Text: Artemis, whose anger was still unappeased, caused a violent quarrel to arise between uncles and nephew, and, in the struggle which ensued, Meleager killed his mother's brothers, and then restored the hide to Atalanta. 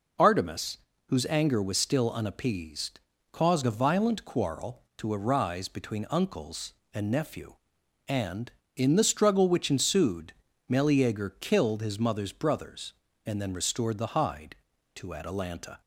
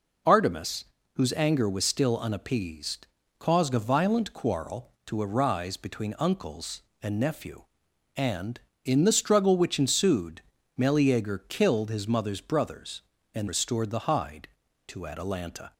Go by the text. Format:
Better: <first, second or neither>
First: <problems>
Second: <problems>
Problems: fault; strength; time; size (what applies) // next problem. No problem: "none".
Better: first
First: none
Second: skips "then"; at 13.4 s